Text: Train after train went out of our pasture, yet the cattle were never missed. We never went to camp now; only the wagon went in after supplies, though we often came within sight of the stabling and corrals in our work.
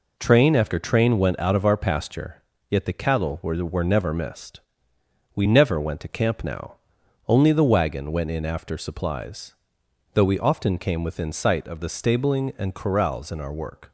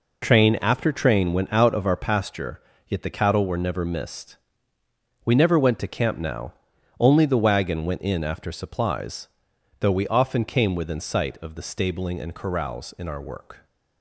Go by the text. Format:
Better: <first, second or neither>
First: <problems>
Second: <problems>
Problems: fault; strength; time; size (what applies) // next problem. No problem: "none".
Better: second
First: says "were" twice; at 3.6 s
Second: none